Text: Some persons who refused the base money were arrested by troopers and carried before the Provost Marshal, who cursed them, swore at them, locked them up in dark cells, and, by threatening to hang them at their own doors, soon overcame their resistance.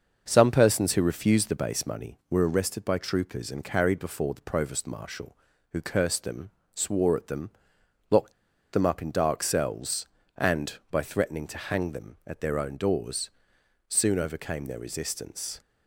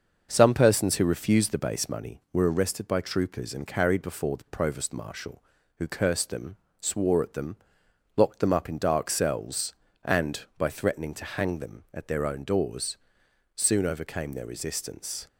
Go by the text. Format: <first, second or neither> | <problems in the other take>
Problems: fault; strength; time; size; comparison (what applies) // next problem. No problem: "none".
second | starts louder than the rest; until 1.2 s; 6.5 dB; also in the second // pauses between "locked" and "them"; at 8.3 s; 0.39 s long